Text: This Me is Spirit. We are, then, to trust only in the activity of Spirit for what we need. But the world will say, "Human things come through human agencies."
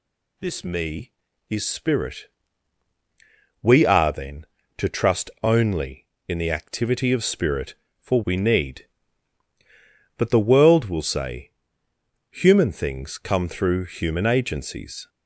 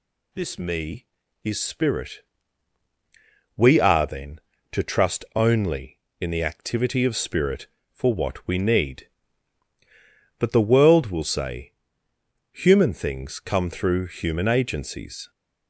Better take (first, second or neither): second